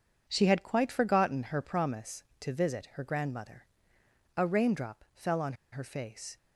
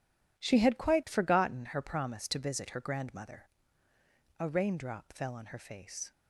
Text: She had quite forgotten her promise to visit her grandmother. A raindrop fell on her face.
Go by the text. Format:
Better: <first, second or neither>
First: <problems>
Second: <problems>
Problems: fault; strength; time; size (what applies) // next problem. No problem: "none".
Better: second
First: pauses between "on" and "her"; slight; at 5.5 s; 0.19 s long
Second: none